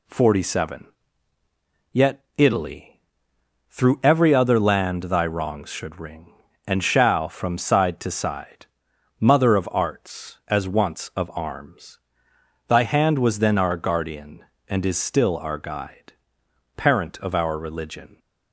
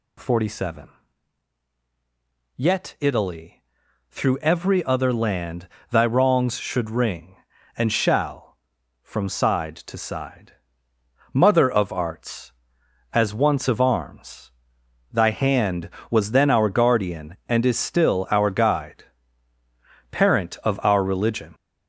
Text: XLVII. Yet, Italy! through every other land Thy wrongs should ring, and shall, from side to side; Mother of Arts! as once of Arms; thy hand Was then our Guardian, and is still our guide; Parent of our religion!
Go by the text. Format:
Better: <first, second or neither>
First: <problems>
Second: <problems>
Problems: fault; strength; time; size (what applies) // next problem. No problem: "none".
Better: first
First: none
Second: gets louder; noticeable; throughout; 5.5 dB // pauses between "land" and "Thy"; slight; at 5.6 s; 0.24 s long